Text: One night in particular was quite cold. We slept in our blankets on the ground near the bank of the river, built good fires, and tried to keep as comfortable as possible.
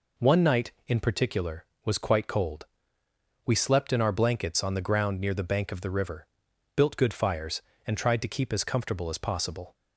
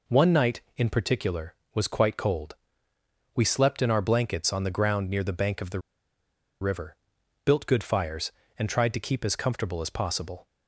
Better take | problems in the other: first | pauses between "the" and "river"; noticeable; at 5.7 s; 0.81 s long

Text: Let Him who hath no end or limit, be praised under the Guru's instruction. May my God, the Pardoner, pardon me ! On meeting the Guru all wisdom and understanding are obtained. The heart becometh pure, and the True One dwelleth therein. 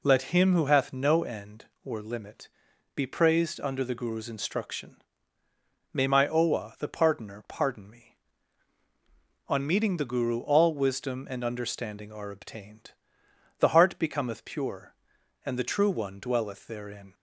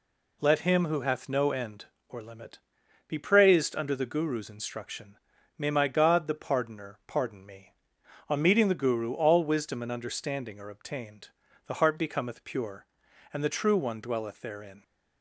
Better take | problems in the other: second | says "Owa" for "God"; at 6.2 s

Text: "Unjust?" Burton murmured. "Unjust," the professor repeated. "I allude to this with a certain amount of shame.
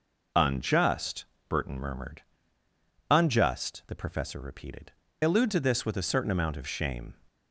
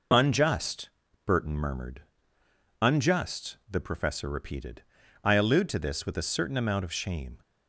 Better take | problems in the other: second | skips "I"; at 5.0 s

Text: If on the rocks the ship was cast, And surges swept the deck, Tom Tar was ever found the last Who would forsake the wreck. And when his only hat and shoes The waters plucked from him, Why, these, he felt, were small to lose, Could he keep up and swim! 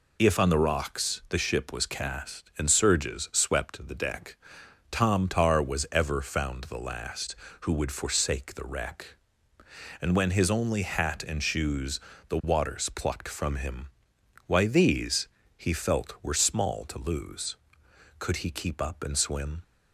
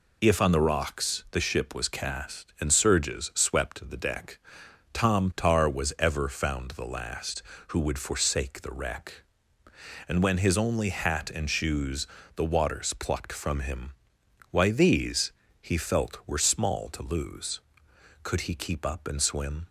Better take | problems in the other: neither | pauses between "shoes" and "The"; slight; the same in both

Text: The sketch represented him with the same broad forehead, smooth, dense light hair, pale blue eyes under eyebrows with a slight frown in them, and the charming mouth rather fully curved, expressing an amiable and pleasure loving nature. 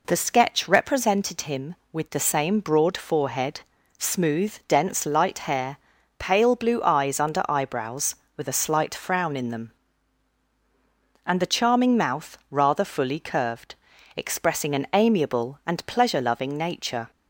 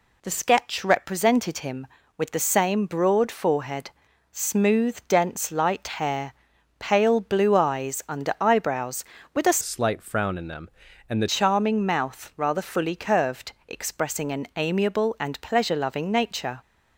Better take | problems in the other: first | pauses between "light" and "hair"; slight; at 5.8 s; 0.16 s long // changes voice from "slight" to "the"; from 9.6 to 11.2 s; 1.6 s long

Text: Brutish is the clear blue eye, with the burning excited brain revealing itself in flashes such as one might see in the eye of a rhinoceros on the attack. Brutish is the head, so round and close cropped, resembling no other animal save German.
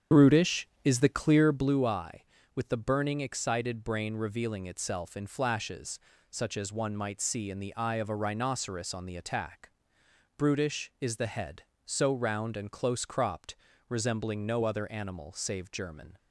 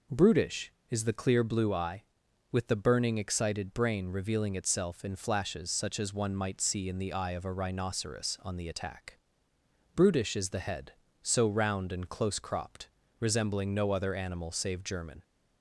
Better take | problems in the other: second | starts louder than the rest; strong; until 1.7 s; 8 dB // pauses between "flashes" and "such"; slight; at 6.0 s; 0.28 s long

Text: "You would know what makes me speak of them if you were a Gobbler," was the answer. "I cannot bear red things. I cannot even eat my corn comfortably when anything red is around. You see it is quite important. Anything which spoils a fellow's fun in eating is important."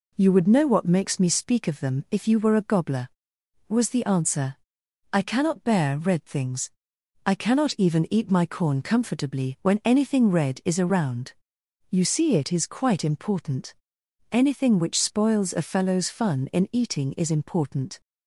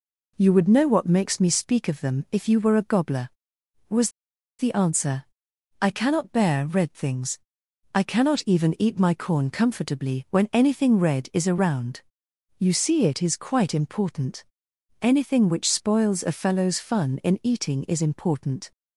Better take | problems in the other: first | pauses between "was" and "the"; noticeable; at 4.0 s; 0.49 s long

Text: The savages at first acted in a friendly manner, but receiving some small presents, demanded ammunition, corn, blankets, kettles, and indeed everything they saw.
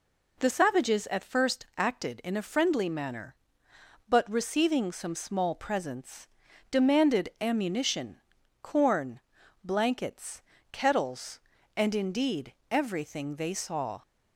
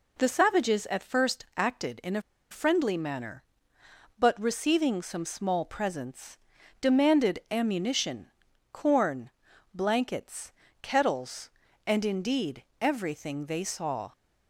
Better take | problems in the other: first | pauses between "a" and "friendly"; slight; at 2.2 s; 0.29 s long // pauses between "indeed" and "everything"; slight; at 12.6 s; 0.18 s long; slight in the first

